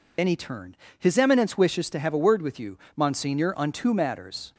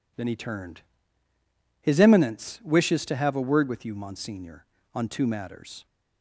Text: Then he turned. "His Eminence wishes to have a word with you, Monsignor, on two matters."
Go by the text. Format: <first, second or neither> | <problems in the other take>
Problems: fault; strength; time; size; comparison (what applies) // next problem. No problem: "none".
second | loses the start of "Then"; at 0.1 s; 45 ms